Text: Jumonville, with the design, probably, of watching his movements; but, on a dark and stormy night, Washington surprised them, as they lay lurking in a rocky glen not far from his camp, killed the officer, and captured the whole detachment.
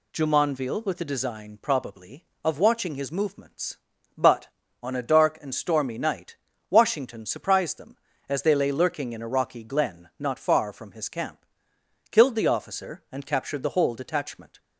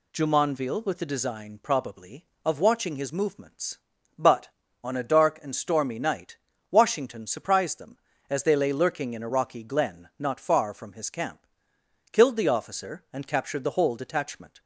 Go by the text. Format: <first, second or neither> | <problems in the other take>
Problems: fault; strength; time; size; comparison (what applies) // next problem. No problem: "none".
neither | none